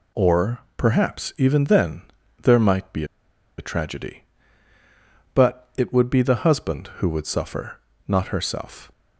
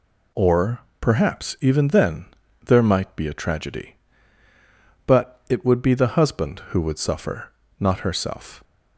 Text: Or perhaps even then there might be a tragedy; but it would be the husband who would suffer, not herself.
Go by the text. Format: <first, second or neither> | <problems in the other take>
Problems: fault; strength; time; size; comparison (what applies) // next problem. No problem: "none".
second | pauses between "Or" and "perhaps"; slight; at 0.5 s; 0.18 s long; slight in the second // pauses between "then" and "there"; at 2.0 s; 0.40 s long; also in the second // pauses between "be" and "a"; noticeable; at 3.0 s; 0.54 s long